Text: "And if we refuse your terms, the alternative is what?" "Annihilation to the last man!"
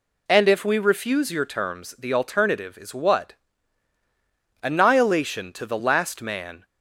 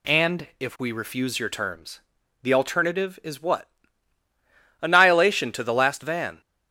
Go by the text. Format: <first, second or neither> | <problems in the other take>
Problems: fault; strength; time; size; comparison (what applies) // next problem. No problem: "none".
first | says "van" for "man"; at 6.0 s